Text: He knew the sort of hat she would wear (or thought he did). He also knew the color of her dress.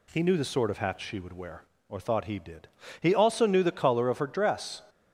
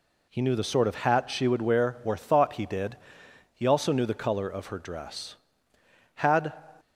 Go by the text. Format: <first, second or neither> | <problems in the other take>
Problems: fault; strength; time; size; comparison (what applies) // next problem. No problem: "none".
first | goes on to say "Had"; slight; from 6.1 s on; 0.38 s long